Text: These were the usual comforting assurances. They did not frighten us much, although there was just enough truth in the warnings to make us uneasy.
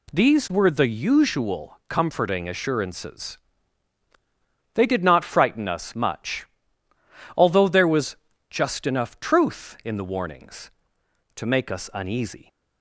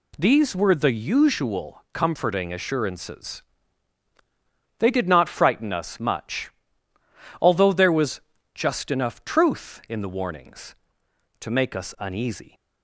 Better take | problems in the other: neither | pauses between "was" and "just"; slight; the same in both

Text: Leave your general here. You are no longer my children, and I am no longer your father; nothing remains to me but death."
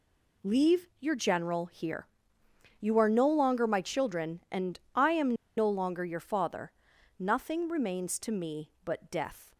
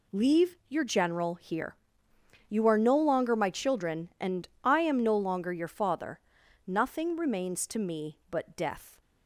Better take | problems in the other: second | pauses between "Leave" and "your"; slight; at 0.8 s; 0.16 s long; slight in the second // pauses between "and" and "I"; slight; at 4.7 s; 0.16 s long; slight in the second // pauses between "am" and "no"; slight; at 5.3 s; 0.23 s long

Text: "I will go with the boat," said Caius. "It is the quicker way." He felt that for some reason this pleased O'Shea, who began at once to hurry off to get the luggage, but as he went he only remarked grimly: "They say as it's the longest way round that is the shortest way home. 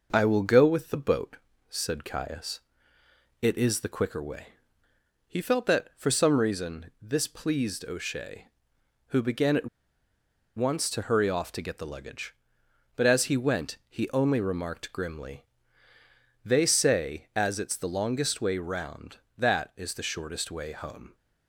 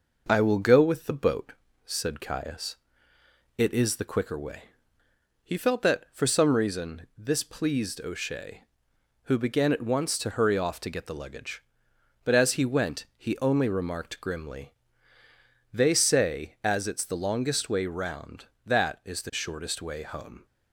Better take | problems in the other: second | pauses between "at" and "once"; noticeable; at 9.6 s; 0.88 s long

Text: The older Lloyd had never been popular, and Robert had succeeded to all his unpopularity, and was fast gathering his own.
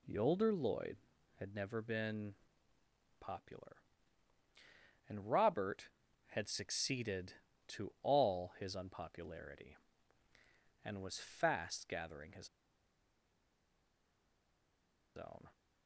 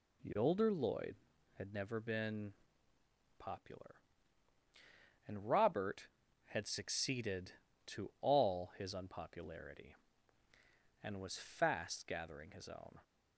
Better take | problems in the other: second | pauses between "been" and "popular"; noticeable; at 2.3 s; 0.86 s long; noticeable in the second // pauses between "his" and "own"; strong; at 12.4 s; 2.6 s long

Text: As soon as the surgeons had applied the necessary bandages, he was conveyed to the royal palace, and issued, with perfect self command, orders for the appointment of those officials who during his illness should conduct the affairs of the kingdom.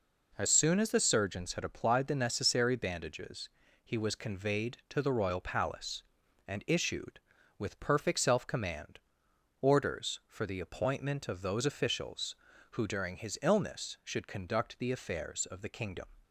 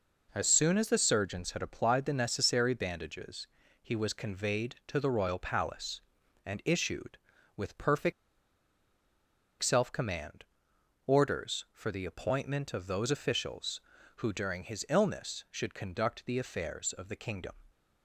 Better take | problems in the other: first | pauses between "perfect" and "self"; strong; at 8.1 s; 1.5 s long

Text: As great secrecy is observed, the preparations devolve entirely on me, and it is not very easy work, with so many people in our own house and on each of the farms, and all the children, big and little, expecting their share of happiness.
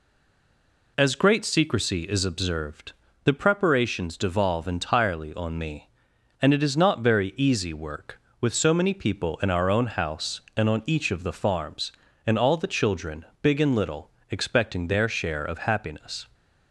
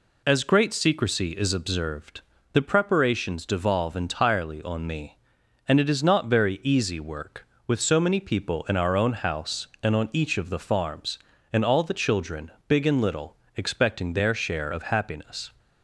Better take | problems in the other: second | stays silent before the first word; slight; until 0.9 s; 0.9 s long

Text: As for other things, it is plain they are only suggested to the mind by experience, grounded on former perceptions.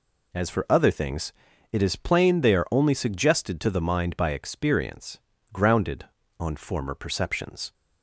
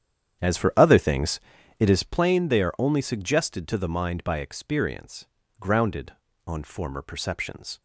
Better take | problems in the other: first | starts louder than the rest; strong; until 2.1 s; 9 dB

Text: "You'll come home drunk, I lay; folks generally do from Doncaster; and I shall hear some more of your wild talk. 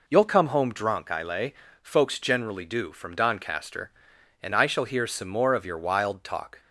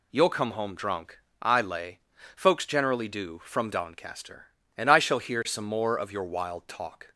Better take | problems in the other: neither | none

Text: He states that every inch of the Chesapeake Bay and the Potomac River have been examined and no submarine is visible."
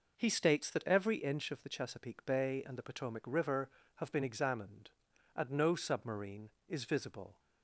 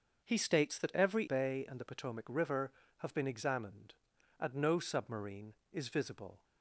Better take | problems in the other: first | starts louder than the rest; until 1.2 s; 6.5 dB // skips "inch of the Chesapeake"; at 1.2 s

